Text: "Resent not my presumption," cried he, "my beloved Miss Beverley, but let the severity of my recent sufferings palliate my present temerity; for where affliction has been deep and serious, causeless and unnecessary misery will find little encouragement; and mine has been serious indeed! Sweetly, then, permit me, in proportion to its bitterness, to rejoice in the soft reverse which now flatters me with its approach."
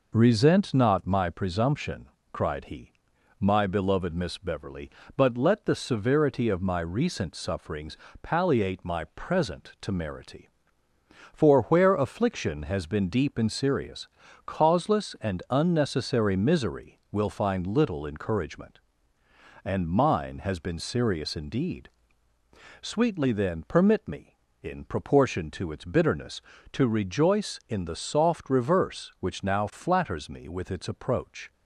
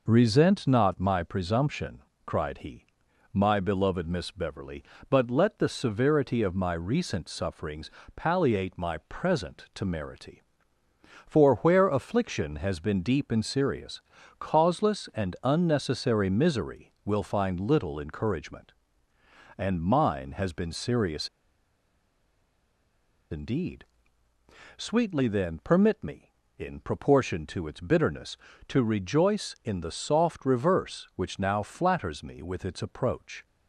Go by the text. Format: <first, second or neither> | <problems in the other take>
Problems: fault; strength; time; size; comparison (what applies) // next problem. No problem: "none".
first | pauses between "sufferings" and "palliate"; slight; at 7.9 s; 0.24 s long; slight in the first // pauses between "serious" and "indeed"; strong; at 21.2 s; 2.0 s long